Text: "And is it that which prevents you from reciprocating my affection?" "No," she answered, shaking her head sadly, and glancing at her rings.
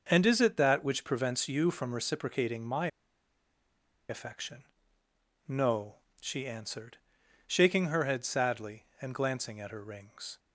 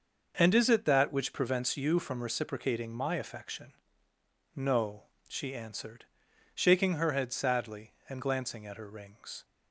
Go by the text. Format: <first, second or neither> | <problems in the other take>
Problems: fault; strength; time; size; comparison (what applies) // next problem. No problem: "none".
second | starts louder than the rest; noticeable; until 1.1 s; 6 dB; noticeable in the second // pauses between "my" and "affection"; at 2.8 s; 1.2 s long